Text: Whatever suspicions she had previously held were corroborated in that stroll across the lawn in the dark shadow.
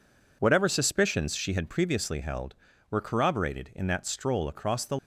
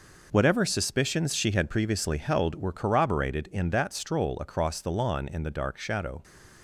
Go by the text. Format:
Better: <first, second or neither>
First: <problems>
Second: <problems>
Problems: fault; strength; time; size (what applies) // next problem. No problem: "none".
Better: second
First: stops before "lawn in the dark shadow"; at 4.9 s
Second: none